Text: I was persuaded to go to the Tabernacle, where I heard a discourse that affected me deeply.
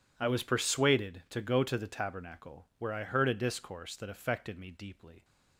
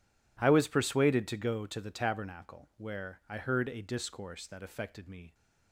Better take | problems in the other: first | stops before "deeply"; at 5.3 s

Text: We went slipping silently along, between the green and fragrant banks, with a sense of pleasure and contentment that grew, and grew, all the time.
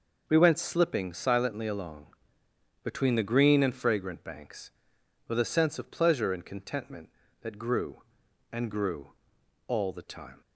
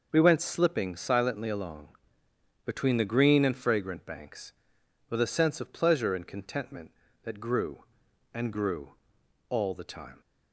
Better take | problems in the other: neither | none

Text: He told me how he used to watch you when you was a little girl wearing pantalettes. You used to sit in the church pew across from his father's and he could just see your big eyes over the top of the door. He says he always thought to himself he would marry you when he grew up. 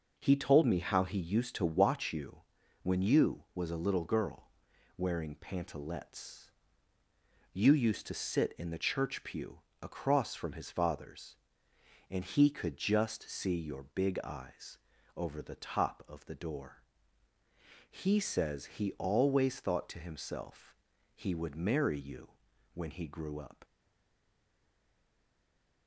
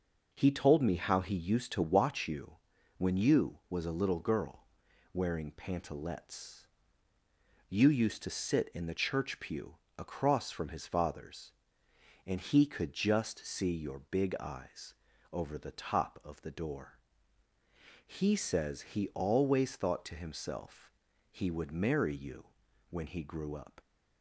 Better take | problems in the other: second | pauses between "you" and "when"; at 2.4 s; 0.42 s long; also in the second // pauses between "girl" and "wearing"; noticeable; at 4.4 s; 0.46 s long; noticeable in the second // pauses between "pew" and "across"; slight; at 9.5 s; 0.22 s long; slight in the second // pauses between "eyes" and "over"; at 14.7 s; 0.38 s long; also in the second // pauses between "himself" and "he"; at 20.7 s; 0.38 s long; also in the second // pauses between "you" and "when"; at 22.3 s; 0.42 s long; also in the second // stays silent after the last word; from 23.6 s on; 2.2 s long

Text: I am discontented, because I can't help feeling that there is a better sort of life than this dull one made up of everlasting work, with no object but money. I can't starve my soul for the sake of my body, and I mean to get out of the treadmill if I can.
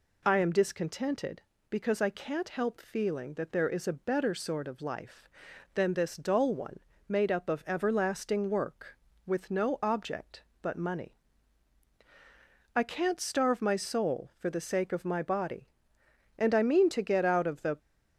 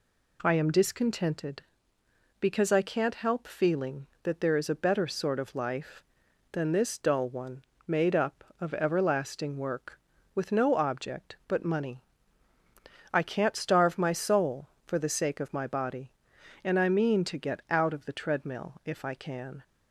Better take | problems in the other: second | pauses between "one" and "made"; slight; at 6.7 s; 0.28 s long; slight in the second // stops before "treadmill if I can"; at 17.7 s

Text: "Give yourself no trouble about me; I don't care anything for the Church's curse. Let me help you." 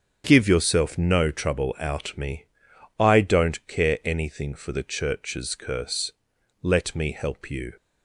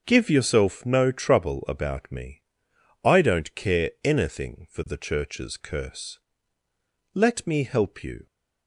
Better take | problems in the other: second | starts louder than the rest; until 1.2 s; 7 dB; also in the second // says "out" for "about"; at 1.7 s

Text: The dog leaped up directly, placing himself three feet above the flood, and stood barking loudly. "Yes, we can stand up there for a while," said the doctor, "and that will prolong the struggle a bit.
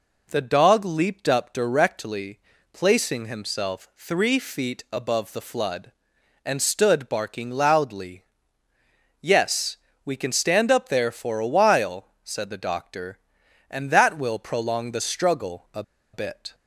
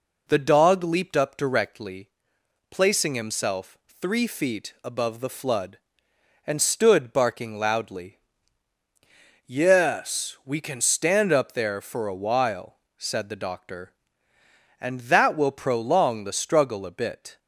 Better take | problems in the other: second | pauses between "a" and "bit"; slight; at 15.8 s; 0.31 s long

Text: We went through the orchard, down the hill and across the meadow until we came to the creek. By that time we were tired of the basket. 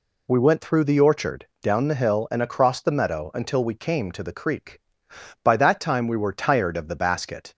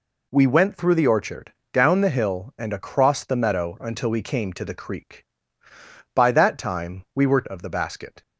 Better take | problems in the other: first | skips "tired"; at 7.4 s

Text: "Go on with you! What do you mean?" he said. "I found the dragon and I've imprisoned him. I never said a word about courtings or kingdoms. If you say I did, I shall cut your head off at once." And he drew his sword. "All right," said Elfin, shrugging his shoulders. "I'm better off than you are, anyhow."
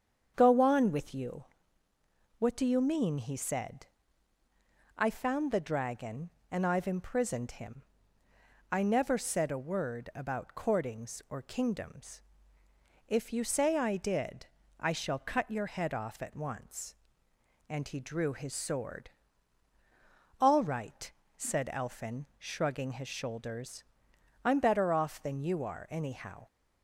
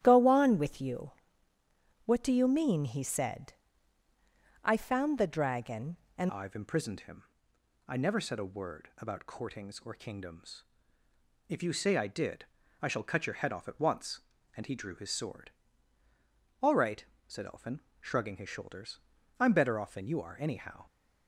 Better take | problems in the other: first | starts louder than the rest; strong; until 1.0 s; 11.5 dB; strong in the first // changes voice at "I've"; from 6.2 s on; 14.6 s long

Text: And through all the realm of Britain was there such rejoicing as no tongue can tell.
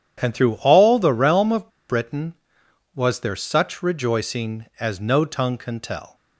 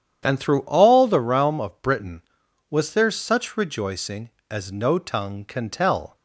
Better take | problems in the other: second | starts louder than the rest; strong; until 1.2 s; 9 dB; strong in the second // pauses between "of" and "Britain"; slight; at 1.6 s; 0.20 s long

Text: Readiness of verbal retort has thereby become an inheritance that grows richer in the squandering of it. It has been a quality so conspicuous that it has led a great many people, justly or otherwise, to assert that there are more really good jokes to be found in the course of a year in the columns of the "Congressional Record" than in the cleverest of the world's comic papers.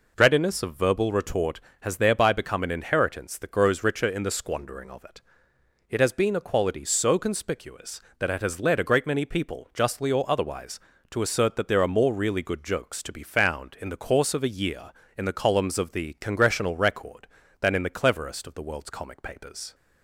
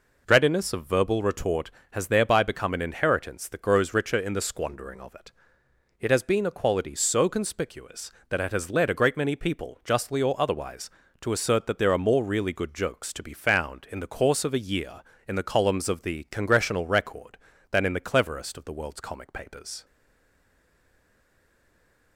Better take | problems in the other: first | stays silent after the last word; from 19.8 s on; 2.3 s long

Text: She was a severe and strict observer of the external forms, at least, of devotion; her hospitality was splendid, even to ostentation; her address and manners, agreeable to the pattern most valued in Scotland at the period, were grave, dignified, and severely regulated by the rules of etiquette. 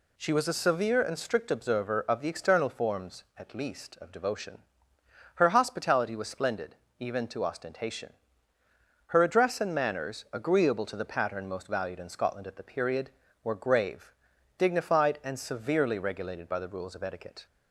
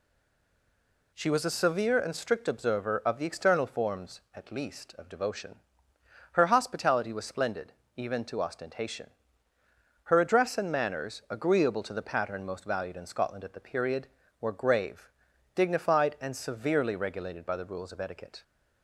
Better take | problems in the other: first | stays silent before the first word; until 1.1 s; 1.1 s long

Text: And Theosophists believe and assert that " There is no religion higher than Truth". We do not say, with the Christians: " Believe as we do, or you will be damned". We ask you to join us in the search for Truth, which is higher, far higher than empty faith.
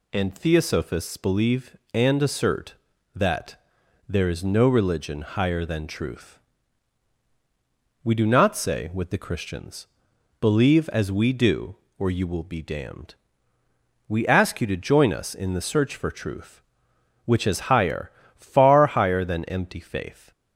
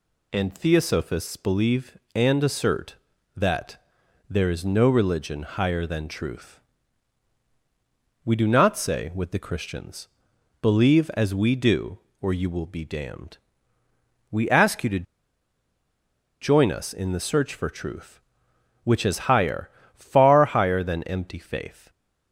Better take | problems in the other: first | pauses between "to" and "join"; strong; at 15.0 s; 1.3 s long

